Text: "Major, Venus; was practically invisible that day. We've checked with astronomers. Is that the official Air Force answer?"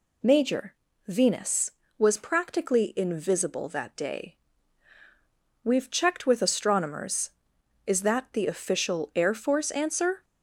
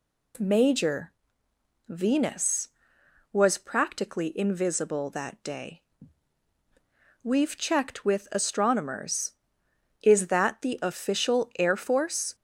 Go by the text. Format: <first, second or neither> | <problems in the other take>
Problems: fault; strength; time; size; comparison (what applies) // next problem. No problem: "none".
first | stops before "answer"; at 12.3 s